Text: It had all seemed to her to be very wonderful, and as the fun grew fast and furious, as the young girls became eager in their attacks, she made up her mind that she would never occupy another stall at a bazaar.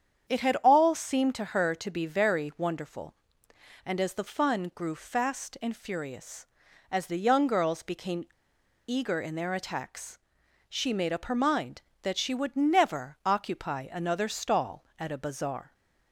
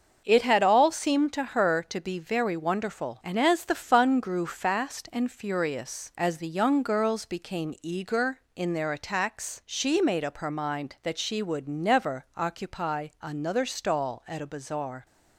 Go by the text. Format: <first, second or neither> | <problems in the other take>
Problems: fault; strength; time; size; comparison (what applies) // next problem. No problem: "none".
second | starts louder than the rest; strong; until 1.3 s; 8 dB; also in the second // pauses between "became" and "eager"; noticeable; at 8.2 s; 0.59 s long